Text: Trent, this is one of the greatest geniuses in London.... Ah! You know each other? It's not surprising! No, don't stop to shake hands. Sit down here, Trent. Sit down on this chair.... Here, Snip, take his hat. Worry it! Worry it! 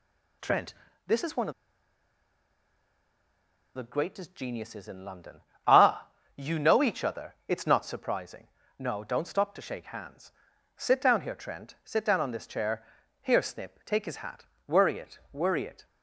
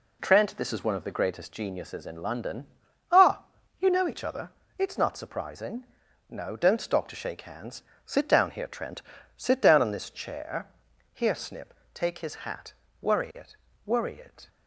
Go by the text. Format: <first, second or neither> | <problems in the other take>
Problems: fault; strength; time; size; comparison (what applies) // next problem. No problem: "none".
second | pauses between "of" and "the"; strong; at 1.5 s; 2.2 s long